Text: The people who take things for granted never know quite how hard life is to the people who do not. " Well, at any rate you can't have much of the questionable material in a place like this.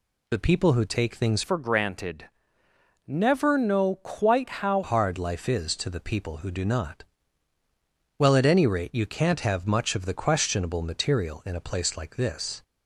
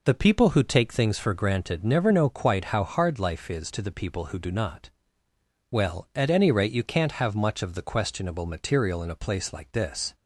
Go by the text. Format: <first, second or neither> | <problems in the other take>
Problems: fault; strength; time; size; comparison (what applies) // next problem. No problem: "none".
second | changes voice from "for" to "how"; from 1.4 to 4.8 s; 3.4 s long // pauses between "granted" and "never"; noticeable; at 2.2 s; 0.78 s long